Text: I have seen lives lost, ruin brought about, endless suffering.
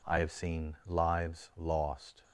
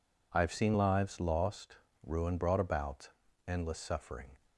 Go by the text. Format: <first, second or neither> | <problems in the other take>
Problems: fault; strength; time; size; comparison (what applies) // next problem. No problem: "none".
second | stops before "ruin brought about endless suffering"; at 2.2 s